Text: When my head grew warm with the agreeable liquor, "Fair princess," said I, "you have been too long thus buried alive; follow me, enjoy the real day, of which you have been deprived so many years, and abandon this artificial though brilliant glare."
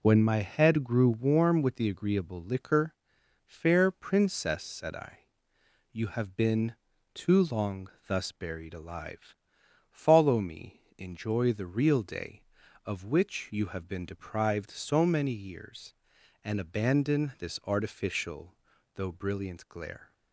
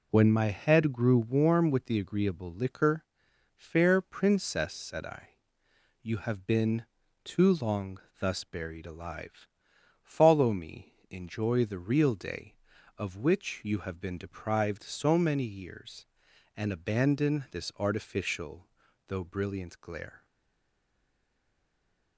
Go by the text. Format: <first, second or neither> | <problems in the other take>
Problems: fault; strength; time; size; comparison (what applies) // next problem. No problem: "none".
first | pauses between "been" and "too"; at 6.8 s; 0.38 s long; also in the first // pauses between "long" and "thus"; slight; at 7.9 s; 0.22 s long; slight in the first // pauses between "artificial" and "though"; at 18.6 s; 0.40 s long; also in the first // stays silent after the last word; noticeable; from 20.2 s on; 1.9 s long